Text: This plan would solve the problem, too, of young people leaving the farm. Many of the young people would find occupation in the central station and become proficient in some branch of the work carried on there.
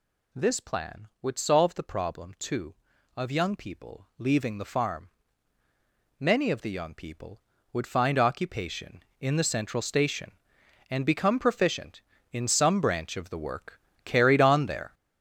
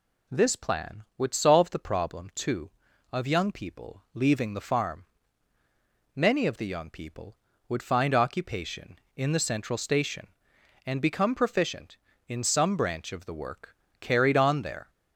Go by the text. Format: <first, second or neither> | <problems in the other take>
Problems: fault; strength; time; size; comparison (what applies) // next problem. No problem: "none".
second | gets louder; strong; throughout; 8 dB // pauses between "work" and "carried"; slight; at 13.7 s; 0.26 s long; slight in the second